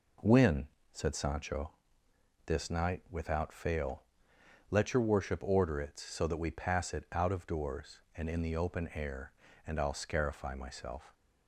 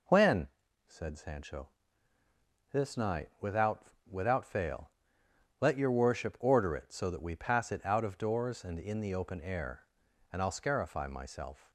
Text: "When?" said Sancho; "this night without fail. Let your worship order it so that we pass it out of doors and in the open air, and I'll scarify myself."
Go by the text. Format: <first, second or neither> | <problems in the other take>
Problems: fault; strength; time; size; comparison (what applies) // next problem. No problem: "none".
first | says "without" twice; at 4.0 s